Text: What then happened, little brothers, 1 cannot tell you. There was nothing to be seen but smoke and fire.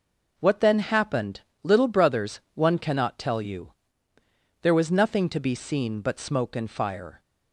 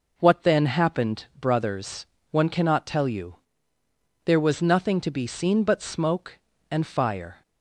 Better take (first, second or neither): first